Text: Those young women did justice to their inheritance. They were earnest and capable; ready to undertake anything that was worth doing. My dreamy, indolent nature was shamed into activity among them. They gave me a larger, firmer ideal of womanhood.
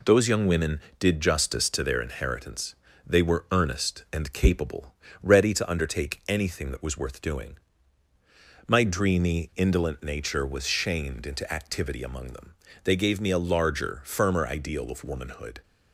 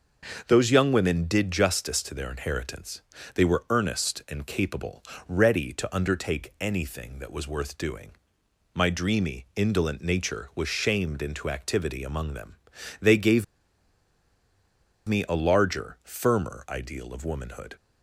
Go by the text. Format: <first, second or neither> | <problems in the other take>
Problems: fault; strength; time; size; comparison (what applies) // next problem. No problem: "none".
first | starts louder than the rest; until 1.4 s; 6 dB // pauses between "gave" and "me"; strong; at 13.4 s; 1.6 s long